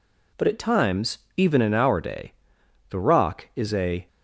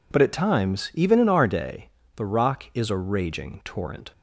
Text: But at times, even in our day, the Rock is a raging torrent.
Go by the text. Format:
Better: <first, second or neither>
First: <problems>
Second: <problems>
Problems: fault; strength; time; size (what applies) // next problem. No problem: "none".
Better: second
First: stops before "raging torrent"; at 4.0 s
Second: none